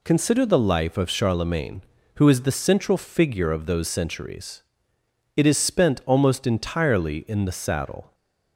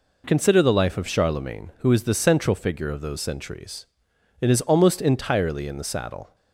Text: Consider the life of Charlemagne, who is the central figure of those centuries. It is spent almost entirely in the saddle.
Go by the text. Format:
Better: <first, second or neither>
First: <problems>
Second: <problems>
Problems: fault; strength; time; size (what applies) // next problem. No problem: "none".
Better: first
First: none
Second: skips "spent"; at 4.6 s